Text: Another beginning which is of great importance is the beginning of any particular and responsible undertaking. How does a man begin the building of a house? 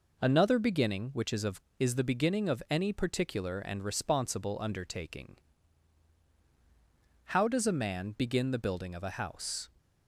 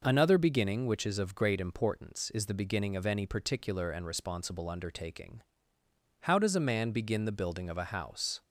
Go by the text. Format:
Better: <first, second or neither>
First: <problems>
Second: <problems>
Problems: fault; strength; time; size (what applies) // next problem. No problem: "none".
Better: second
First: skips "great importance"; at 1.6 s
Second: none